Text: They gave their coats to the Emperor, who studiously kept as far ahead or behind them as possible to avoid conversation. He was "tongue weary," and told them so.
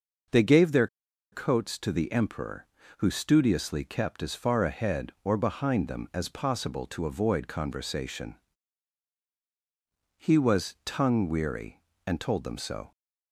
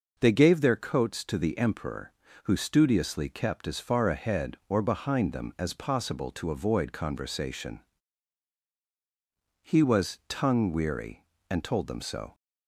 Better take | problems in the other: second | pauses between "their" and "coats"; noticeable; at 0.8 s; 0.46 s long

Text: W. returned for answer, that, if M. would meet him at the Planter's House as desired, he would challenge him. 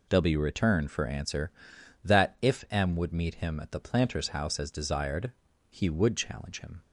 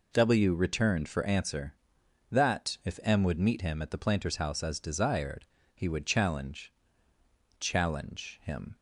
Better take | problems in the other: first | says "challenge" twice; at 7.6 s

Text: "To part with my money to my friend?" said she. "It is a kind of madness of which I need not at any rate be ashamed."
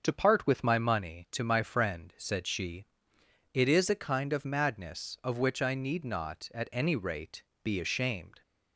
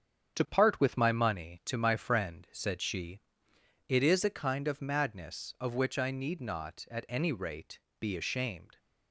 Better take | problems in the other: first | gets quieter; throughout; 6 dB // starts louder than the rest; strong; until 1.4 s; 8 dB; also in the first // pauses between "rate" and "be"; slight; at 7.7 s; 0.22 s long; slight in the first

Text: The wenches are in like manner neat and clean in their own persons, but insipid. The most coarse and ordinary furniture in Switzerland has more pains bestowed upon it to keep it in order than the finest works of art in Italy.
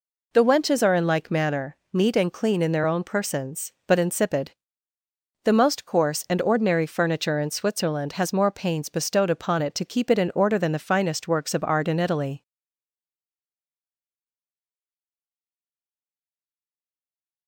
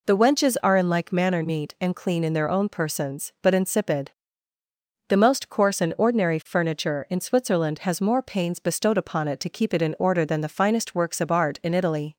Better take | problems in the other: second | pauses between "manner" and "neat"; slight; at 1.7 s; 0.16 s long // stays silent after the last word; strong; from 12.4 s on; 5.0 s long

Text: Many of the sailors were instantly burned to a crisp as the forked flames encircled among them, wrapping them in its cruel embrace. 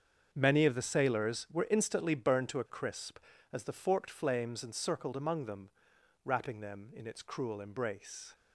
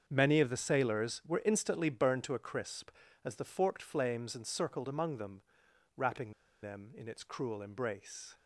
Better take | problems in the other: first | starts louder than the rest; until 1.0 s; 7 dB; also in the first // pauses between "wrapping" and "them"; slight; at 6.3 s; 0.32 s long

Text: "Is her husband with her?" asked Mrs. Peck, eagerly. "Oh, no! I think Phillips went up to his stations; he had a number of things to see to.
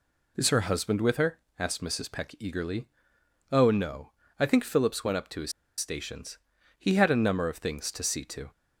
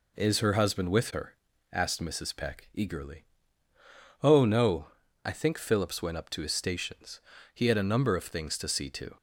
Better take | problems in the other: second | pauses between "his" and "stations"; slight; at 5.5 s; 0.26 s long

